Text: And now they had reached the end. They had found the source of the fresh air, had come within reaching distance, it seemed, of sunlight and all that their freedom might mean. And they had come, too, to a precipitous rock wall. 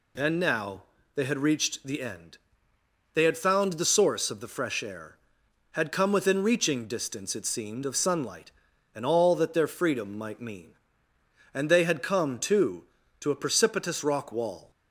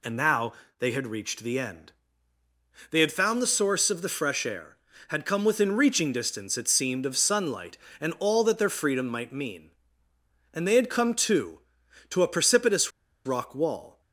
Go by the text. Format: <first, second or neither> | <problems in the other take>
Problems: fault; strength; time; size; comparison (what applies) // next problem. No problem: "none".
first | pauses between "now" and "they"; slight; at 0.5 s; 0.26 s long; slight in the first // pauses between "precipitous" and "rock"; at 12.9 s; 0.36 s long